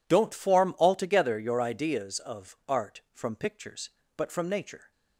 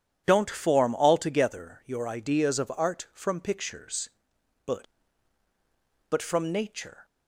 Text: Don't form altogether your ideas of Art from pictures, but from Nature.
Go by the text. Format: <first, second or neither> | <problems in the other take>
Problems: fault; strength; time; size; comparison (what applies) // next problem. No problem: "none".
first | says "but" twice; at 6.0 s